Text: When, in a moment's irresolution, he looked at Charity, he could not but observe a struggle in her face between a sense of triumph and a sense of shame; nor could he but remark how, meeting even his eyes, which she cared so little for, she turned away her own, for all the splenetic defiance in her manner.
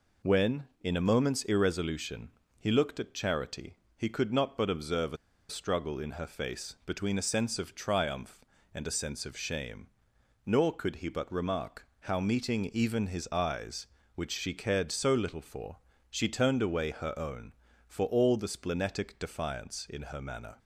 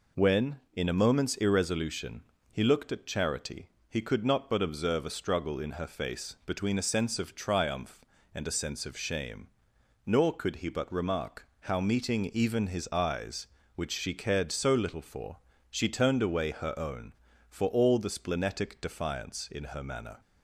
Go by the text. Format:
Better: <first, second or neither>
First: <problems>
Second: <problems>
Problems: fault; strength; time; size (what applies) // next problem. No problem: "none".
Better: second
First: pauses between "a" and "struggle"; slight; at 5.1 s; 0.33 s long // pauses between "remark" and "how"; slight; at 11.8 s; 0.16 s long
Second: pauses between "remark" and "how"; slight; at 11.4 s; 0.16 s long